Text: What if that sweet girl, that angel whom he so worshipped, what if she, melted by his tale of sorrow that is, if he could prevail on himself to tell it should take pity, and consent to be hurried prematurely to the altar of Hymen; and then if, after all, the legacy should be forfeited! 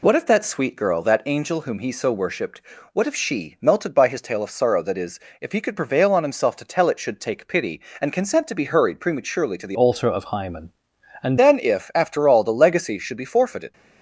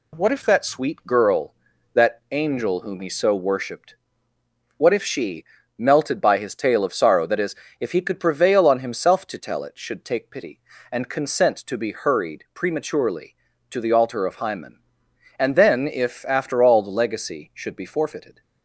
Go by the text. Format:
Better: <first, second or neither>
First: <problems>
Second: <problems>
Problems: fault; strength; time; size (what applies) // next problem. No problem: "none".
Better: second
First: changes voice from "altar" to "and"; from 9.7 to 11.3 s; 1.6 s long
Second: none